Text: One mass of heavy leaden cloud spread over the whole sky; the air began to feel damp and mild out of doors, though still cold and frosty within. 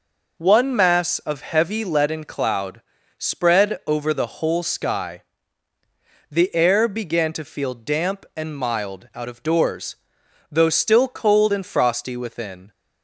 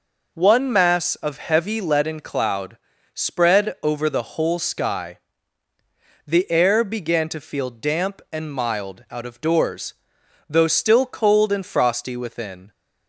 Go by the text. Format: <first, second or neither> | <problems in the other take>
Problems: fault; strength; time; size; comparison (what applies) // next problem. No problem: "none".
neither | pauses between "cloud" and "spread"; slight; the same in both